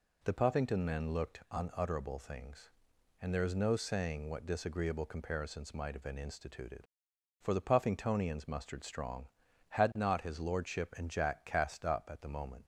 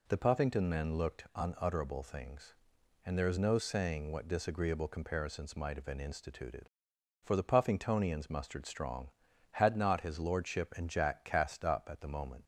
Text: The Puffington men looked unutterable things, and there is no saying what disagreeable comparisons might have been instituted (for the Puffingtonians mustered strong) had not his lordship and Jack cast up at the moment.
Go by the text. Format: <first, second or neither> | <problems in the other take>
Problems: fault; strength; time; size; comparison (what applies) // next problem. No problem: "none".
neither | none